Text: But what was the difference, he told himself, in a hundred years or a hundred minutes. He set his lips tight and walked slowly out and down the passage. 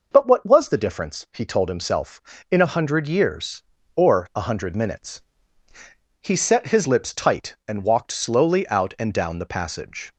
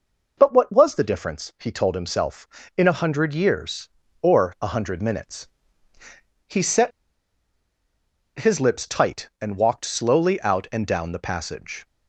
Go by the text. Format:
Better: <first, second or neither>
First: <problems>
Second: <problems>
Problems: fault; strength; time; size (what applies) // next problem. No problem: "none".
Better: first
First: none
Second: pauses between "set" and "his"; strong; at 6.9 s; 1.4 s long